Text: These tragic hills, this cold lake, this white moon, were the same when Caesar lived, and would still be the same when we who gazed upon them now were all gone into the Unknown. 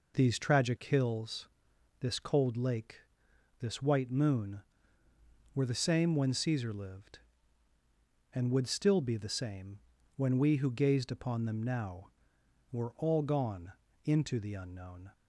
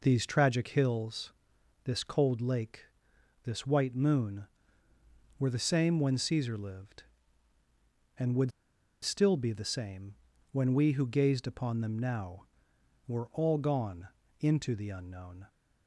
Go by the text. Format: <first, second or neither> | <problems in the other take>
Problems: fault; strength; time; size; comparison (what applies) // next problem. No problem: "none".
first | pauses between "would" and "still"; noticeable; at 8.5 s; 0.51 s long // pauses between "same" and "when"; at 10.1 s; 0.38 s long; also in the first // pauses between "gone" and "into"; slight; at 14.0 s; 0.30 s long; slight in the first